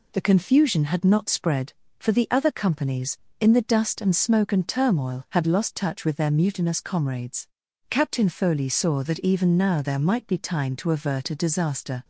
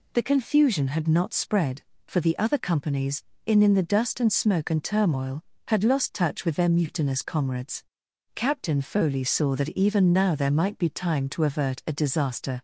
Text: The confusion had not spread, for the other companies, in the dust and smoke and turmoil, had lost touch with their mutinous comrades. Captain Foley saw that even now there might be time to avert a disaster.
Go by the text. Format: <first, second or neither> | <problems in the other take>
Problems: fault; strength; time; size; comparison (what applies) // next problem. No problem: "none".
first | says "in" twice; at 3.6 s